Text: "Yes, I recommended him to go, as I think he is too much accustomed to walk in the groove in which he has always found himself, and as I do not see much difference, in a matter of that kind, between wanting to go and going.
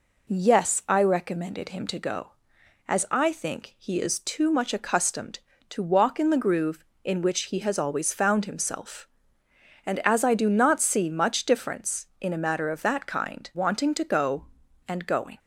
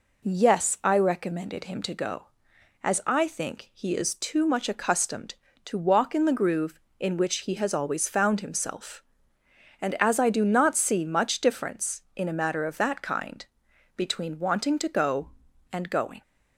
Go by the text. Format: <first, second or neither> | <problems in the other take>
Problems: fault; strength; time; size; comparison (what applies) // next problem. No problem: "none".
second | skips "between"; at 13.5 s